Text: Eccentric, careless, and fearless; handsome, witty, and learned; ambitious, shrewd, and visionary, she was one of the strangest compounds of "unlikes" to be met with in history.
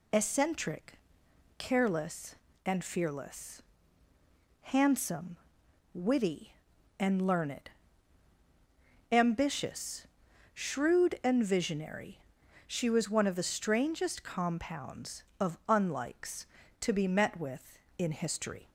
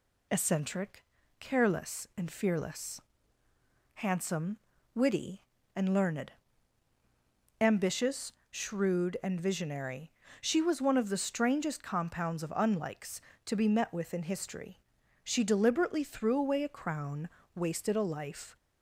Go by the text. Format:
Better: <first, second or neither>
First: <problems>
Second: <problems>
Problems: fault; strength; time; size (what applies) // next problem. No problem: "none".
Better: first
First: none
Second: goes on to say "She deliberately threw away a crown wasted a life"; strong; from 15.2 s on; 3.3 s long